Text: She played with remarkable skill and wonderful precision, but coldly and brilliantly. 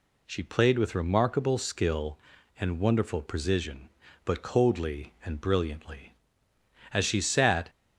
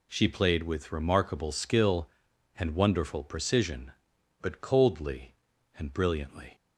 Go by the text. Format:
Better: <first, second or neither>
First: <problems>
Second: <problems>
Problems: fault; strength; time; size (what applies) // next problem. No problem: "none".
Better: second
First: goes on to say "As she sat"; noticeable; from 6.9 s on; 0.78 s long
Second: none